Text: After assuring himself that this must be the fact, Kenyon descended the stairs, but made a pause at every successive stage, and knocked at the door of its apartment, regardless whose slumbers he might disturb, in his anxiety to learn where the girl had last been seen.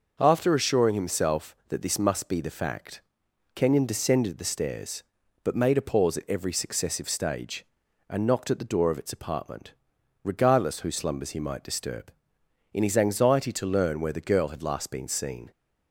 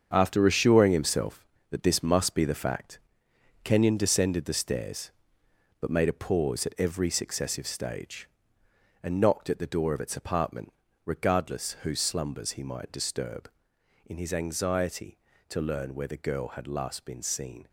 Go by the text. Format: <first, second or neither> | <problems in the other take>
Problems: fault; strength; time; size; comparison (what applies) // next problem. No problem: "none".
first | gets quieter; strong; throughout; 9 dB // starts louder than the rest; strong; until 1.1 s; 7 dB; noticeable in the first